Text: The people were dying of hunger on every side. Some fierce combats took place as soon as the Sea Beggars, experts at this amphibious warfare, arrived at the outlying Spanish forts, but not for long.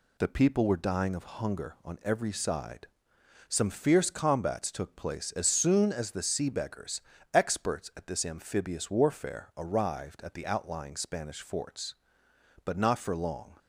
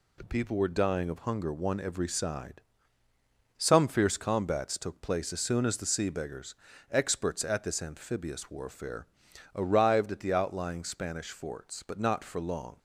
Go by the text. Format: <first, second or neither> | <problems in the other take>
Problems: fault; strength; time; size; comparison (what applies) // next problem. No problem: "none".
first | says "one" for "on"; at 1.5 s